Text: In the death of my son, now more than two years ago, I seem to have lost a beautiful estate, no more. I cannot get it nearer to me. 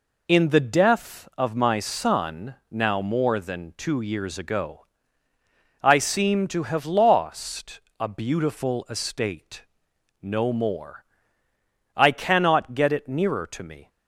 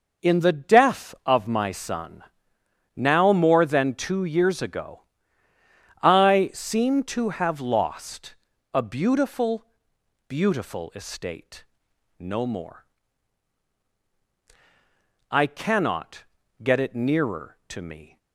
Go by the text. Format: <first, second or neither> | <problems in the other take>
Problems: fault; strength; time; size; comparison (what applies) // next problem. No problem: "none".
first | pauses between "lost" and "a"; at 8.3 s; 0.38 s long; slight in the first // says "beautiful" twice; at 10.2 s // pauses between "cannot" and "get"; at 16.2 s; 0.38 s long